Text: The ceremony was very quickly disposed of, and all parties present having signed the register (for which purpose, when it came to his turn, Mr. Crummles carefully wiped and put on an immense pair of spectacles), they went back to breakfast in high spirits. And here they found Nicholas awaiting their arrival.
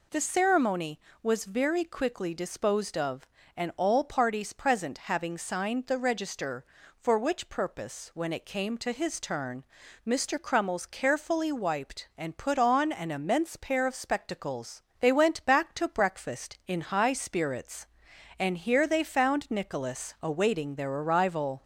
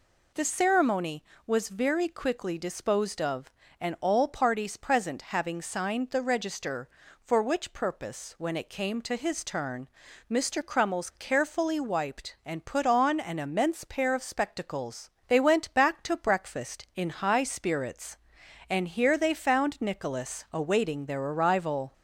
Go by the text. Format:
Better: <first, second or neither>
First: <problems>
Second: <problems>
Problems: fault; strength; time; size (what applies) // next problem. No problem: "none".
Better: neither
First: none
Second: none